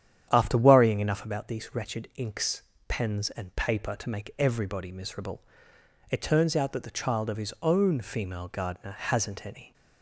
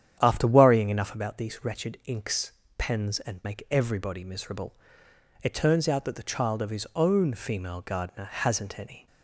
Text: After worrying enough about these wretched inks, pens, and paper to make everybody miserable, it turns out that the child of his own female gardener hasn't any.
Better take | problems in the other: first | starts louder than the rest; strong; until 1.2 s; 9.5 dB; strong in the first // skips "paper to"; at 3.4 s

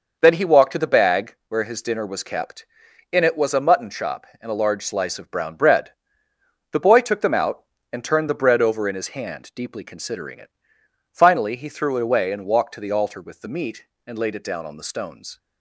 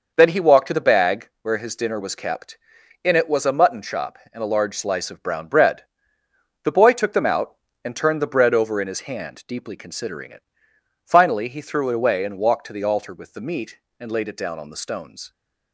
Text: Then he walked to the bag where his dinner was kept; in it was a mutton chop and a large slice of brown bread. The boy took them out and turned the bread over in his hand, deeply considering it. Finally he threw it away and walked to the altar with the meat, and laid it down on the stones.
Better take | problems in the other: neither | none

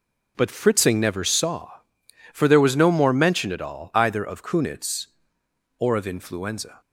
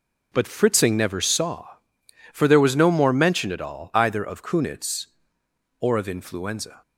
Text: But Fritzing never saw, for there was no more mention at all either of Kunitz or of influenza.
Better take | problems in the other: neither | starts louder than the rest; the same in both

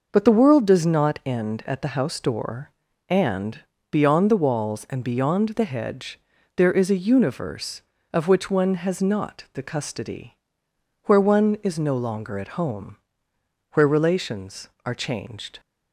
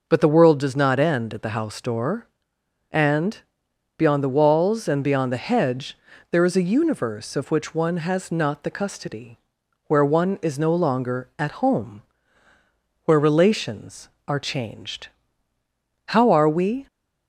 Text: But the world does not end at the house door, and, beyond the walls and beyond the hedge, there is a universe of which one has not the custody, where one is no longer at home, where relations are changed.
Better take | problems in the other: first | goes on to say "How are we"; noticeable; from 16.0 s on; 0.78 s long

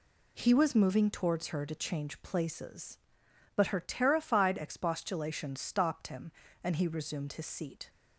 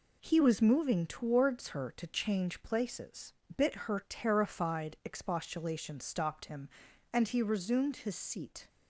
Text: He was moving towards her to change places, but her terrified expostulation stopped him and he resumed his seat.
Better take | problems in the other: first | says "bit" for "but"; at 3.5 s

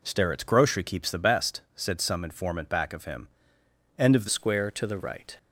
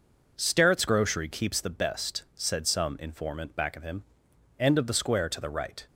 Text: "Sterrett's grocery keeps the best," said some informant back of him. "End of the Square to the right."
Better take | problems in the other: second | changes voice at "Square"; from 4.2 s on; 1.1 s long

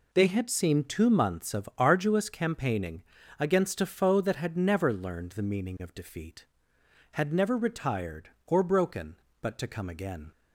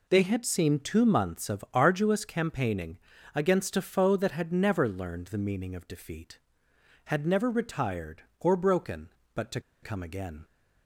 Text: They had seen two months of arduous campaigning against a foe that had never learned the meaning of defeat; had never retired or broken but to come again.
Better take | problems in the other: first | pauses between "campaigning" and "against"; at 2.9 s; 0.38 s long; also in the first // pauses between "to" and "come"; slight; at 9.5 s; 0.23 s long

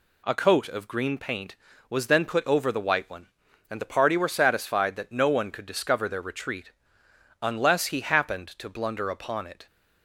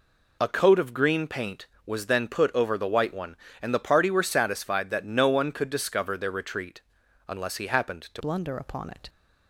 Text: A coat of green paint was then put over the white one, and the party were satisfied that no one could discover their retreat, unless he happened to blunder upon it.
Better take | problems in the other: first | changes voice at "blunder"; from 8.1 s on; 0.9 s long

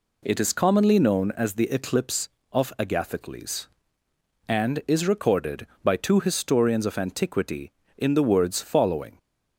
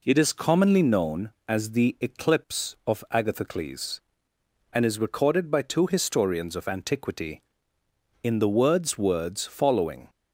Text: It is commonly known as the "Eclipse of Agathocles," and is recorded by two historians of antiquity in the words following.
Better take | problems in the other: first | says "words" twice; at 8.9 s

